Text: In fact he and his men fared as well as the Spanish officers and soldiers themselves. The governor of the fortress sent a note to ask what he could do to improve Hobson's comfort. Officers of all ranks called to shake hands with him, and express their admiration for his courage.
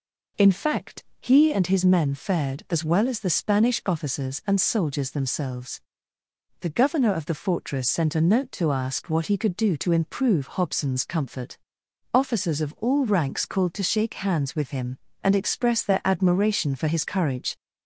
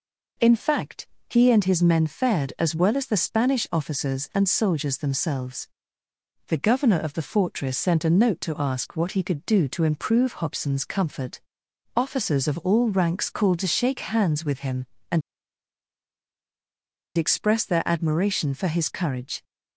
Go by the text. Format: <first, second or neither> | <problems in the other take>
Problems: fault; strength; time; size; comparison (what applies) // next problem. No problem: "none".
first | pauses between "fact" and "he"; slight; at 1.0 s; 0.22 s long; slight in the first // pauses between "and" and "express"; strong; at 15.2 s; 1.9 s long